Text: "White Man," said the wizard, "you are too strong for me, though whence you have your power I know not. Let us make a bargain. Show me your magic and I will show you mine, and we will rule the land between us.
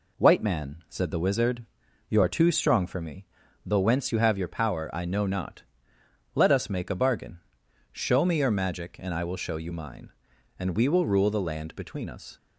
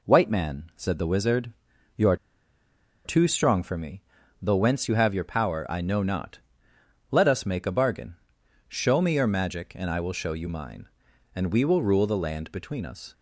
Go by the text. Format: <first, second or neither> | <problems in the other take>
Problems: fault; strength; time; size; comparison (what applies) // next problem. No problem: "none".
first | pauses between "are" and "too"; noticeable; at 2.1 s; 0.89 s long